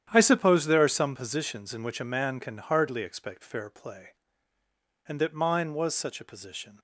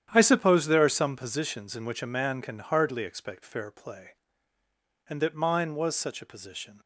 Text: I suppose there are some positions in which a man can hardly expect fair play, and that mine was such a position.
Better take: neither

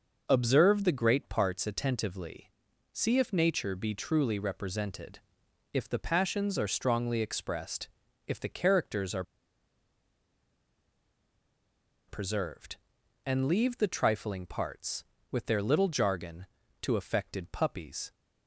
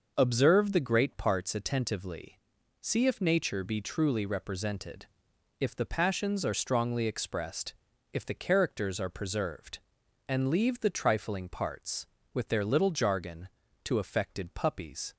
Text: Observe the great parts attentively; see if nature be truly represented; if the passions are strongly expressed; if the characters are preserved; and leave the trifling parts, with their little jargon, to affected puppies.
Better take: second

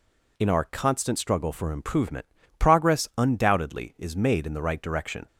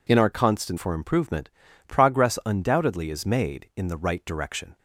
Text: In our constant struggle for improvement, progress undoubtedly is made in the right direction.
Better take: first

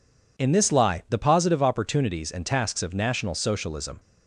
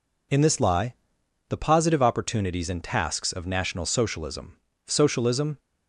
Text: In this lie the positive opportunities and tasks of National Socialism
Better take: first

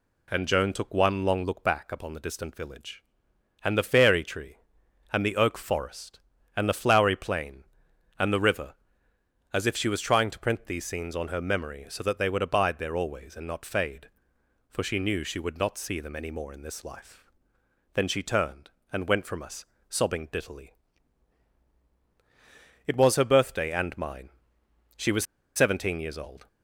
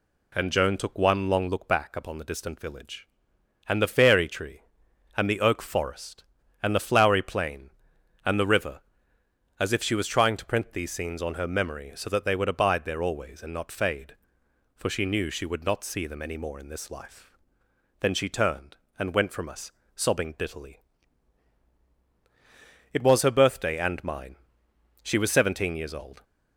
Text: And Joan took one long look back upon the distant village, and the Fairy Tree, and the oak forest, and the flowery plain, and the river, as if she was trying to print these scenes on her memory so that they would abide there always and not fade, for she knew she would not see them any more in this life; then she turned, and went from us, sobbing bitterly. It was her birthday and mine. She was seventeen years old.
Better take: second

